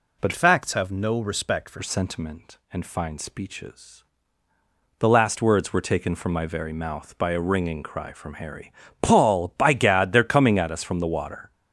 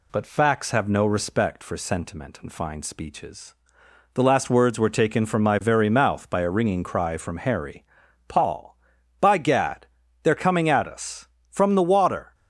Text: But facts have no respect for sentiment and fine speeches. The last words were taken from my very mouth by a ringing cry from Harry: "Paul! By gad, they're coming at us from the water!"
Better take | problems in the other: second | changes voice from "facts" to "for"; from 0.3 to 1.7 s; 1.4 s long

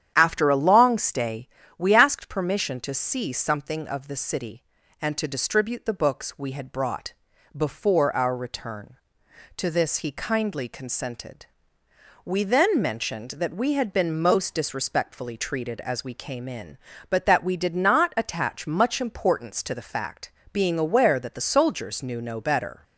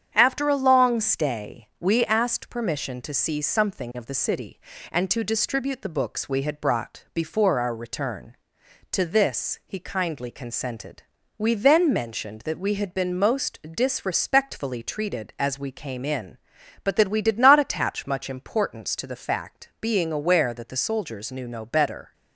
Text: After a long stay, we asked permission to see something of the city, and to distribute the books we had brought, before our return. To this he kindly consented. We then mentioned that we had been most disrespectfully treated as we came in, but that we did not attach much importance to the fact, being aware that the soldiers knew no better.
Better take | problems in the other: neither | starts louder than the rest; strong; the same in both

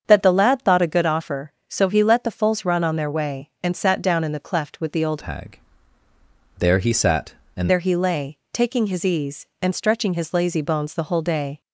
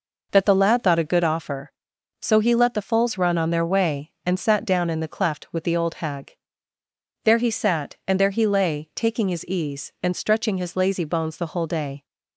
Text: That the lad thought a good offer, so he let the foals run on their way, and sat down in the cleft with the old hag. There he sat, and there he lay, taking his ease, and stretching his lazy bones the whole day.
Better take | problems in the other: second | starts louder than the rest; strong; until 1.0 s; 7.5 dB // changes voice from "hag" to "and"; from 5.2 to 7.7 s; 2.5 s long

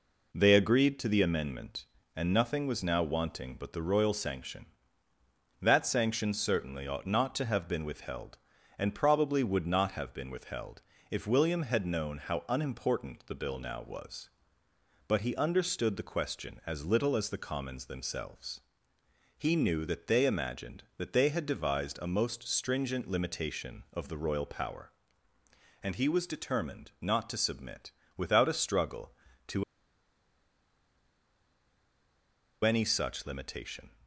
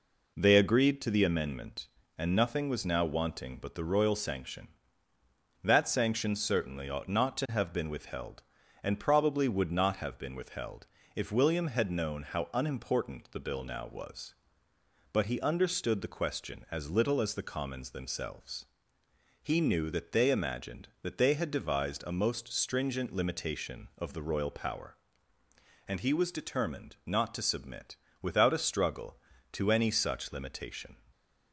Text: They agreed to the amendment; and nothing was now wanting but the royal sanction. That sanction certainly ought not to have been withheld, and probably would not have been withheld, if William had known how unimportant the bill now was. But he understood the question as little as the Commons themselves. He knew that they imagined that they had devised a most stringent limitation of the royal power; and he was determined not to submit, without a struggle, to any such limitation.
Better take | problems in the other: second | pauses between "to" and "any"; strong; at 29.6 s; 3.0 s long

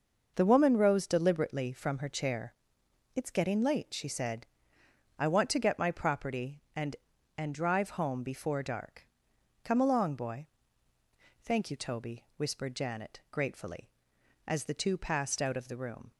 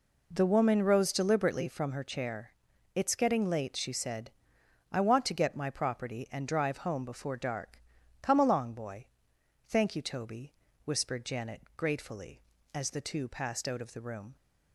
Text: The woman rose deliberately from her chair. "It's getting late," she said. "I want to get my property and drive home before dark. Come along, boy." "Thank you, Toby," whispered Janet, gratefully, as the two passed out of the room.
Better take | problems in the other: second | says "and" twice; at 7.3 s

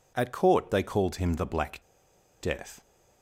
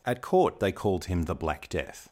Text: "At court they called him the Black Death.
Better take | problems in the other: second | pauses between "Black" and "Death"; noticeable; at 1.8 s; 0.62 s long

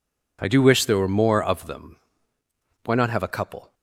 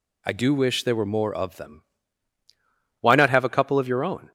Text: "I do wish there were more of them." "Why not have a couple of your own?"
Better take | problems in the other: second | stops before "of your own"; at 3.7 s

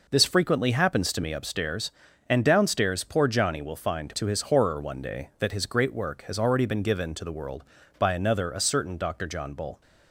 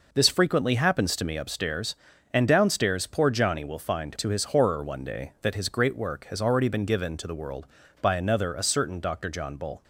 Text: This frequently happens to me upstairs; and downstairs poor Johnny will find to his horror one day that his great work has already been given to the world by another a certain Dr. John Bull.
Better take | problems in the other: neither | none

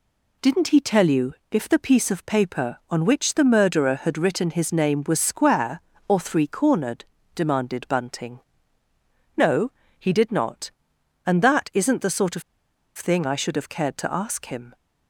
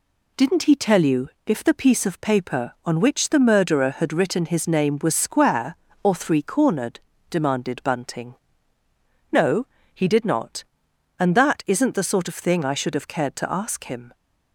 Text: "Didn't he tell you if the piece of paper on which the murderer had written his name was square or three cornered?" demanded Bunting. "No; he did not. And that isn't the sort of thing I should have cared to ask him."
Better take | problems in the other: second | pauses between "you" and "if"; slight; at 1.3 s; 0.16 s long; slight in the second // pauses between "of" and "thing"; noticeable; at 12.4 s; 0.54 s long

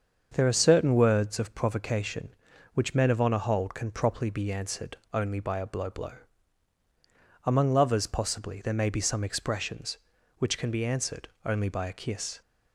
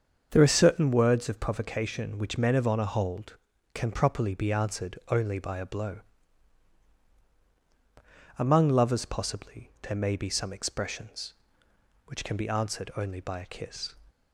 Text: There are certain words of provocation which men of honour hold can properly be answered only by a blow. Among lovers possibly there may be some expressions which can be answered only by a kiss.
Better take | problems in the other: second | starts louder than the rest; until 1.3 s; 6.5 dB; also in the second // pauses between "answered" and "only"; slight; at 4.9 s; 0.16 s long // says "blow" twice; at 5.9 s // pauses between "answered" and "only"; slight; at 11.2 s; 0.18 s long

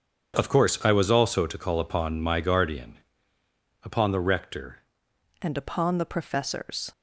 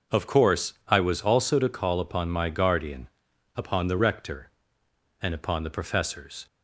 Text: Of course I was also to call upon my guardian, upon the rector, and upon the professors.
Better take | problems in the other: second | starts louder than the rest; strong; until 1.4 s; 7.5 dB // changes voice at "and"; from 5.4 s on; 1.5 s long

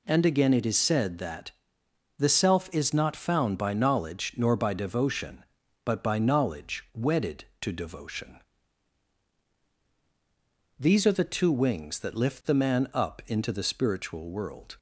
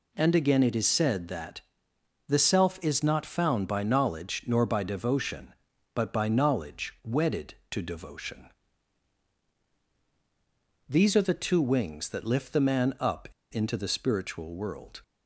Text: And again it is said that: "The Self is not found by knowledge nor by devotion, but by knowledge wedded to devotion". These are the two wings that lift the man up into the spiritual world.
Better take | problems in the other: first | pauses between "up" and "into"; slight; at 13.2 s; 0.22 s long

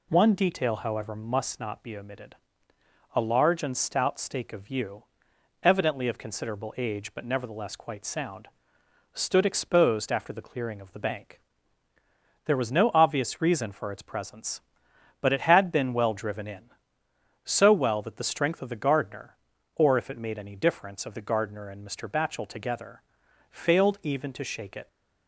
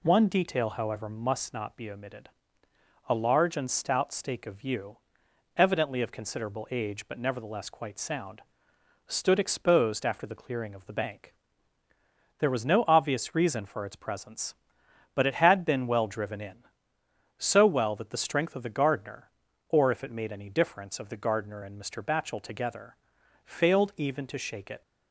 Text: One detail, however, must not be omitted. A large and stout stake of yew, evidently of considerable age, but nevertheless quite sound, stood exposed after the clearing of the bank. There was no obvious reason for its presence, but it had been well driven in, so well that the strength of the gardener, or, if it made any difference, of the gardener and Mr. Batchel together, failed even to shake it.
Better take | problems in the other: neither | none

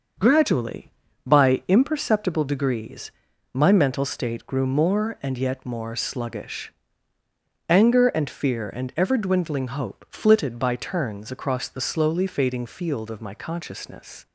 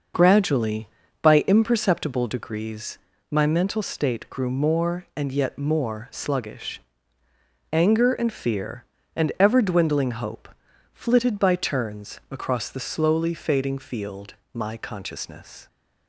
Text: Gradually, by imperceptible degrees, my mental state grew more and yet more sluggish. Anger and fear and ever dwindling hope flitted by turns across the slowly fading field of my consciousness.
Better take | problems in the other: first | starts louder than the rest; until 1.5 s; 6 dB; also in the first // pauses between "hope" and "flitted"; noticeable; at 10.4 s; 0.46 s long // skips "of"; at 14.4 s

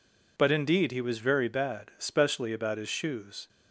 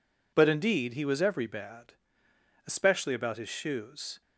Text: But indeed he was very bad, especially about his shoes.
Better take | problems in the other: first | says "every" for "very"; at 1.2 s

